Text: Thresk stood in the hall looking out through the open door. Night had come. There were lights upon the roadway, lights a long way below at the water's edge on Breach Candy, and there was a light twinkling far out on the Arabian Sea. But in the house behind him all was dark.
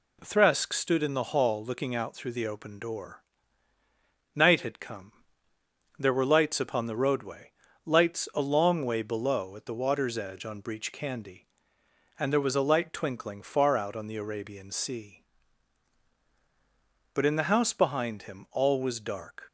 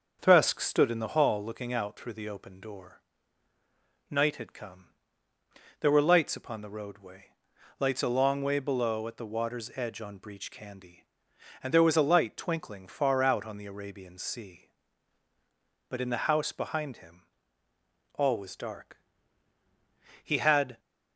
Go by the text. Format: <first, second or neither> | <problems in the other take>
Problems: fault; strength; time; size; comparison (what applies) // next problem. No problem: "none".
first | starts louder than the rest; until 1.2 s; 6.5 dB // pauses between "him" and "all"; noticeable; at 17.2 s; 0.94 s long // goes on to say "He had"; from 20.2 s on; 0.56 s long